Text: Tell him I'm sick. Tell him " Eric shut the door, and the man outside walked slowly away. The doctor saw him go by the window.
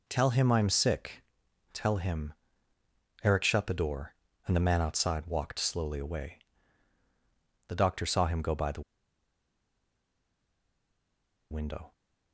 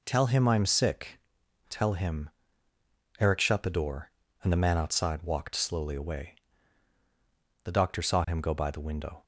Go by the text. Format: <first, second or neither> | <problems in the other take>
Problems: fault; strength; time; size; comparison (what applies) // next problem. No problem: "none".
second | pauses between "the" and "window"; strong; at 8.8 s; 2.7 s long